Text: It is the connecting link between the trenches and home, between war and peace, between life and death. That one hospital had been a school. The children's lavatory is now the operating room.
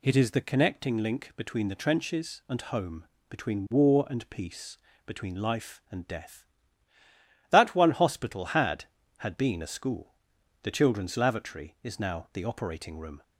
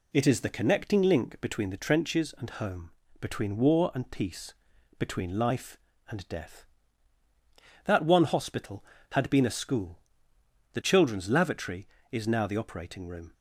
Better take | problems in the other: second | says "had" twice; at 9.1 s

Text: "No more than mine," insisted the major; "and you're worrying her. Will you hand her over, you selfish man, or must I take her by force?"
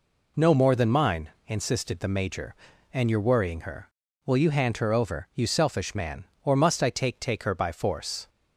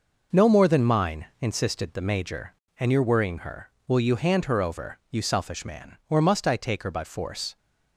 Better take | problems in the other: second | says "take" twice; at 7.1 s

